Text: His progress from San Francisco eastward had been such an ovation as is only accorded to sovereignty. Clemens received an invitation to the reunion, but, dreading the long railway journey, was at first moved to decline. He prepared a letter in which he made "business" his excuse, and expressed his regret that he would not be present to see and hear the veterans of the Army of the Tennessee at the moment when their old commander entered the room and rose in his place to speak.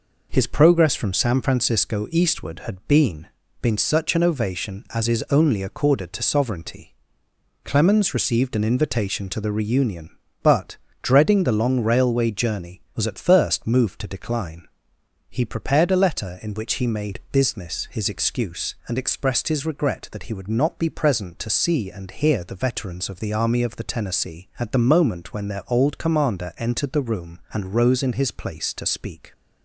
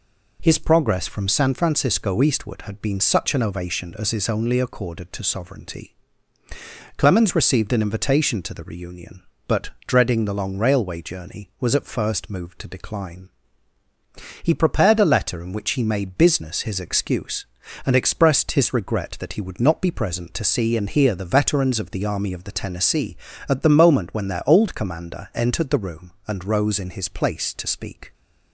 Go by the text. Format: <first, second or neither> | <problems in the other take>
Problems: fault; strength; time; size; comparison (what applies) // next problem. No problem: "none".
second | says "been" twice; at 3.6 s